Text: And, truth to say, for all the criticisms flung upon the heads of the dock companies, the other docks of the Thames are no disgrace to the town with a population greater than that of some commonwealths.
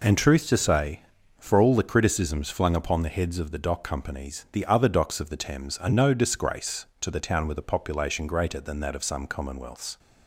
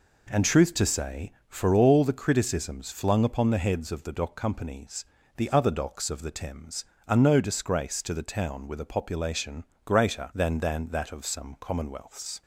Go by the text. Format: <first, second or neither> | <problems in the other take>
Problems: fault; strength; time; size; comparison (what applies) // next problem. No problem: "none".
first | pauses between "population" and "greater"; slight; at 9.6 s; 0.22 s long // says "than" twice; at 10.5 s